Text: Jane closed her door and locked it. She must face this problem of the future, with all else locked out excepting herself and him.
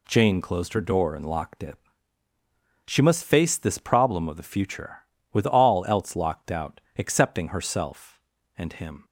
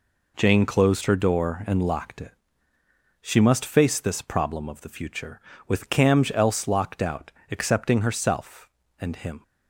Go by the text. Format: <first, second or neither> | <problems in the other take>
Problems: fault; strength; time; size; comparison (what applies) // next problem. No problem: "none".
first | says "camj" for "all"; at 5.9 s // pauses between "out" and "excepting"; slight; at 7.3 s; 0.20 s long; slight in the first